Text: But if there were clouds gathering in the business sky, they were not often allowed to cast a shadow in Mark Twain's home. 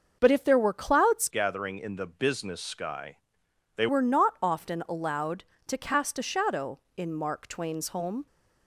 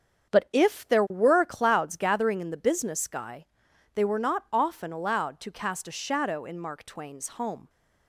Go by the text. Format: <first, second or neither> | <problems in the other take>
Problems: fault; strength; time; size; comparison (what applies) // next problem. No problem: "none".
second | starts louder than the rest; noticeable; until 1.2 s; 6 dB; strong in the second // changes voice from "gathering" to "they"; from 1.2 to 3.8 s; 2.6 s long